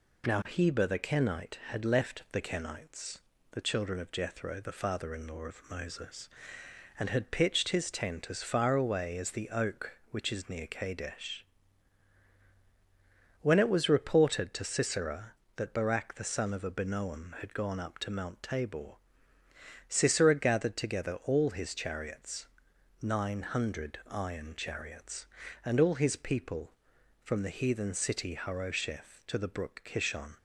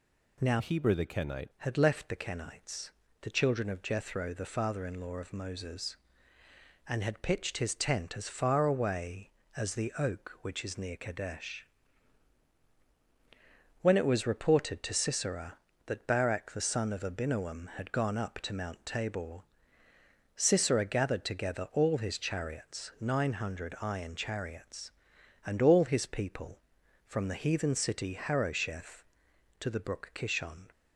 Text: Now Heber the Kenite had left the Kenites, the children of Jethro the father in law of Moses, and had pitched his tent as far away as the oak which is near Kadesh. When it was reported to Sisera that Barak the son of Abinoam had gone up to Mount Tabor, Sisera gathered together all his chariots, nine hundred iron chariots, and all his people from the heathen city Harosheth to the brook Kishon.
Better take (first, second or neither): first